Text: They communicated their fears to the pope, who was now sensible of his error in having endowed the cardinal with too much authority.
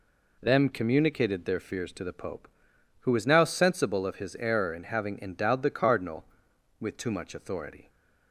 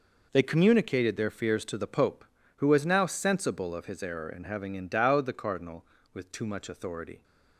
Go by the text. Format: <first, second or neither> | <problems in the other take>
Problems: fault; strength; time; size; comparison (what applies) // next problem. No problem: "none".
second | says "Them" for "They"; at 0.4 s